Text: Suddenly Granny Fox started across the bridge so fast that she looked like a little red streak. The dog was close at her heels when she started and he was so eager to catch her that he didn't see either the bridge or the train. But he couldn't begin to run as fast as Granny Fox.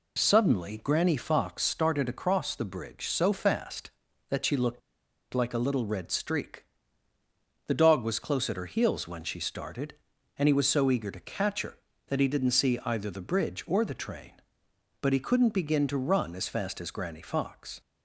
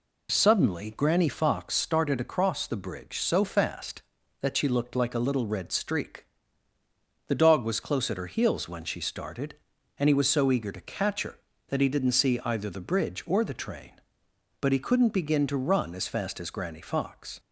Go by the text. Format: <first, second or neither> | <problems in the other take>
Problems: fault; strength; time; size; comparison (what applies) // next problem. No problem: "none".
second | pauses between "looked" and "like"; noticeable; at 4.8 s; 0.53 s long